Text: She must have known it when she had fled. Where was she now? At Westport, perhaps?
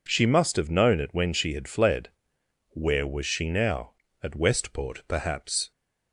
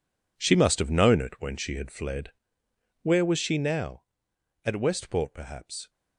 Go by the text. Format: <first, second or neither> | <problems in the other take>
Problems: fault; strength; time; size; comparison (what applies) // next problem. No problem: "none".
first | gets quieter; strong; throughout; 12.5 dB